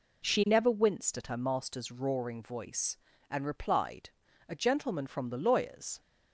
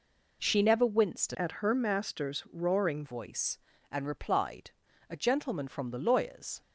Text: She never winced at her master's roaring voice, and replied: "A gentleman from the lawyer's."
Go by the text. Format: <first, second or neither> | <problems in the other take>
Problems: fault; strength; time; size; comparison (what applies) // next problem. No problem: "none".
first | changes voice from "at" to "roaring"; from 1.3 to 3.0 s; 1.7 s long